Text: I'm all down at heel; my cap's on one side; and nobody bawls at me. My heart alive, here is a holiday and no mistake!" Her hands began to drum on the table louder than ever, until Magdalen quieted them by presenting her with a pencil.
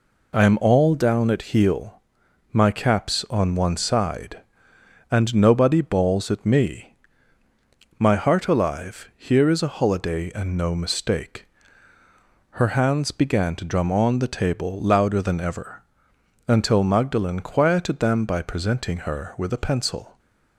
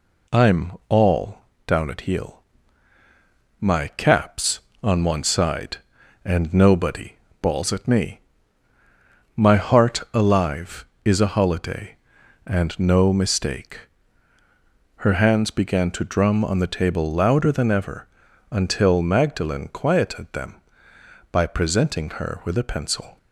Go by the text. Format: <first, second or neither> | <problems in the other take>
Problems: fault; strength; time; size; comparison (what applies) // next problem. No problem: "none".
first | pauses between "I'm" and "all"; slight; at 0.7 s; 0.18 s long // pauses between "all" and "down"; slight; at 1.3 s; 0.28 s long // pauses between "nobody" and "bawls"; slight; at 7.1 s; 0.24 s long // skips "here"; at 10.9 s